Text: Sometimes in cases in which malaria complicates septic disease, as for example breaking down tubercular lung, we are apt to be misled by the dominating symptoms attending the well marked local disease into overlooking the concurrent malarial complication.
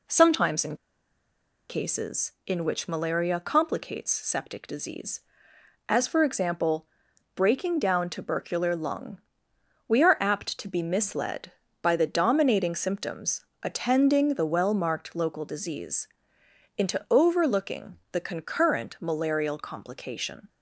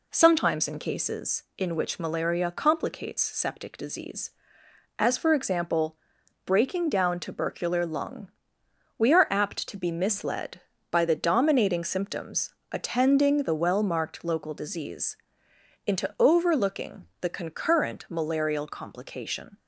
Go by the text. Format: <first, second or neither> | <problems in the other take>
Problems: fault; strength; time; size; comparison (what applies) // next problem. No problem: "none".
second | pauses between "in" and "cases"; noticeable; at 0.7 s; 0.93 s long // pauses between "example" and "breaking"; noticeable; at 6.8 s; 0.50 s long; noticeable in the second // pauses between "symptoms" and "attending"; slight; at 13.4 s; 0.18 s long; slight in the second // pauses between "disease" and "into"; noticeable; at 16.0 s; 0.68 s long; noticeable in the second